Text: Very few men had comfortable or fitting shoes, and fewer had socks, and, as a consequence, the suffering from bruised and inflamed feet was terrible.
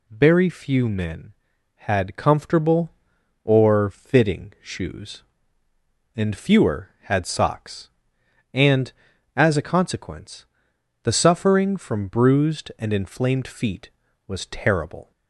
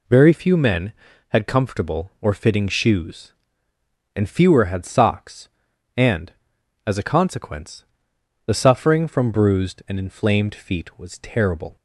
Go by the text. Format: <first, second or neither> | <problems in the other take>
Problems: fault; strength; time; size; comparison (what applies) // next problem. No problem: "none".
neither | none